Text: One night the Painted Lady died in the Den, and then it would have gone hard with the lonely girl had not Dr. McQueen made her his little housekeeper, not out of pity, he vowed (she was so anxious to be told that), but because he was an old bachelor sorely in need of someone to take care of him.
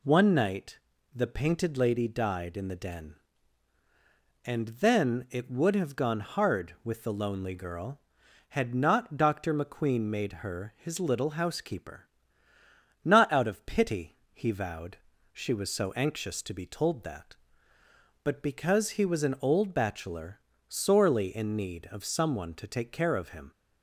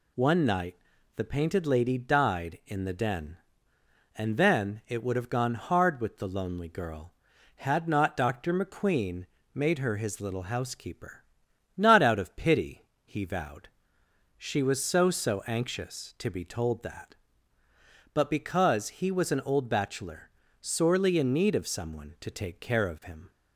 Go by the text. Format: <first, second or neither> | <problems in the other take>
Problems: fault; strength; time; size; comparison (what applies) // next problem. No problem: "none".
first | pauses between "night" and "the"; at 0.7 s; 0.40 s long; slight in the first // pauses between "McQueen" and "made"; slight; at 9.2 s; 0.28 s long // says "so" twice; at 15.1 s // pauses between "bachelor" and "sorely"; slight; at 20.2 s; 0.30 s long; slight in the first